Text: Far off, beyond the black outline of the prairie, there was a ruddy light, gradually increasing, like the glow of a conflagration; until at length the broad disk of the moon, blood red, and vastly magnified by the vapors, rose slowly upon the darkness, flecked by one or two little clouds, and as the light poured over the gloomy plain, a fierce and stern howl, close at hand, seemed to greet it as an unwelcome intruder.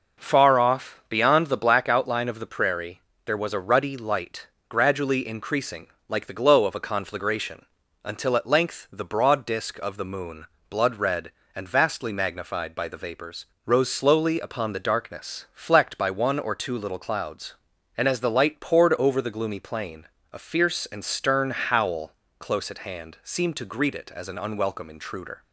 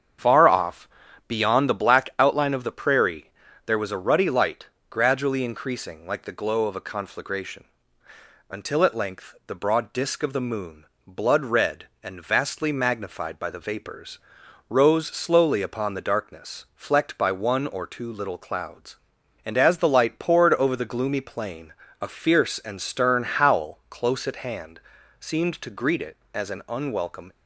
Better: first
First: none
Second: starts louder than the rest; strong; until 1.6 s; 8 dB // stops before "intruder"; at 27.3 s

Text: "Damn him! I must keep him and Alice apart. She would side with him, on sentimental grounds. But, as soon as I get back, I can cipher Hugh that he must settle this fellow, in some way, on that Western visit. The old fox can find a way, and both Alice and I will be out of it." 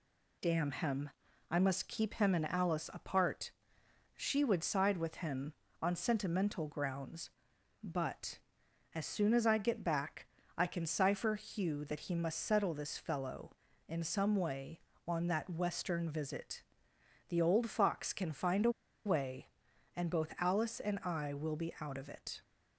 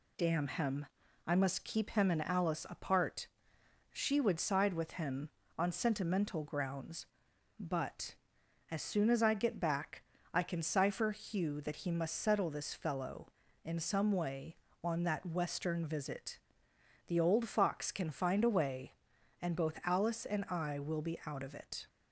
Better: second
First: pauses between "a" and "way"; slight; at 18.7 s; 0.34 s long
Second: none

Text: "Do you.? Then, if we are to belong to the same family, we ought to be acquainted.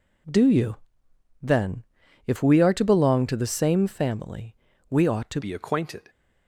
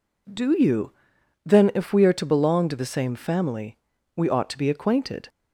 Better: second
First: changes voice at "be"; from 5.4 s on; 0.6 s long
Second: none

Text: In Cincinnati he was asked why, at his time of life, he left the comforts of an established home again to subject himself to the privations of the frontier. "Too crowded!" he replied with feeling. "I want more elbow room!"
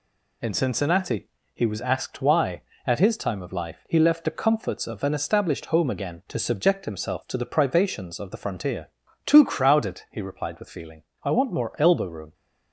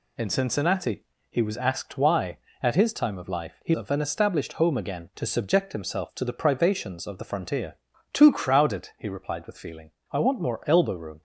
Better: first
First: pauses between "Cincinnati" and "he"; slight; at 1.2 s; 0.24 s long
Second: pauses between "Cincinnati" and "he"; slight; at 1.0 s; 0.24 s long // skips "left the comforts"; at 3.7 s

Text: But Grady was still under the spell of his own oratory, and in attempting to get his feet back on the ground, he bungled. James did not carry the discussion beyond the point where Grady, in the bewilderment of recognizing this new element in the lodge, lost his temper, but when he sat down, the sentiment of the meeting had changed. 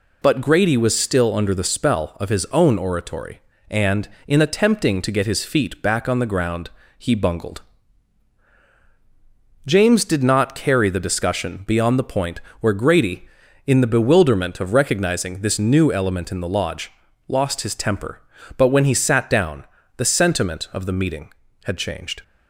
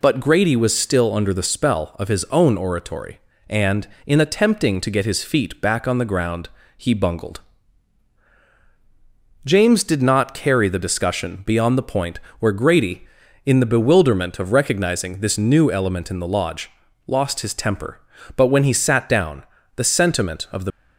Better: first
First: pauses between "point" and "where"; slight; at 12.4 s; 0.20 s long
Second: pauses between "point" and "where"; slight; at 12.1 s; 0.20 s long // stops before "meeting had changed"; at 20.7 s

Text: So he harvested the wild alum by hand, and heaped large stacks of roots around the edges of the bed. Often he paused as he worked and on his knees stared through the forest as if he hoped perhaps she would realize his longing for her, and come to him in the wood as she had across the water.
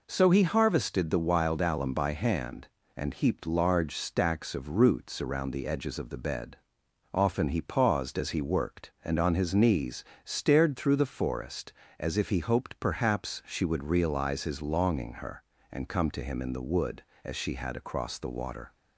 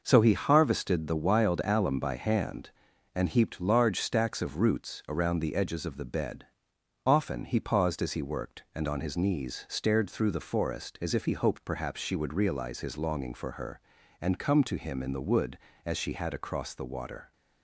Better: second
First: pauses between "knees" and "stared"; slight; at 10.0 s; 0.20 s long // skips "for"; at 15.1 s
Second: none

